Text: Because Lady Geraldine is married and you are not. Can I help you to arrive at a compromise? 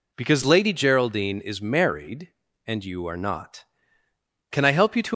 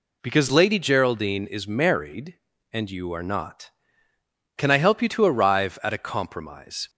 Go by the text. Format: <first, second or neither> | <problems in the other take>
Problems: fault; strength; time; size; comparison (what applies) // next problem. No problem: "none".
second | stops before "arrive at a compromise"; at 5.1 s